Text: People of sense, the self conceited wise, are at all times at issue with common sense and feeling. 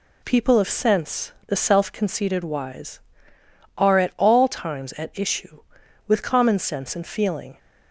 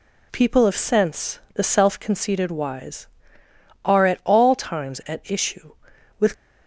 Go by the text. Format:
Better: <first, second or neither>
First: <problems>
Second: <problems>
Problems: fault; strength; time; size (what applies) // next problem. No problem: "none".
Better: first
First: none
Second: stops before "common sense and feeling"; at 6.3 s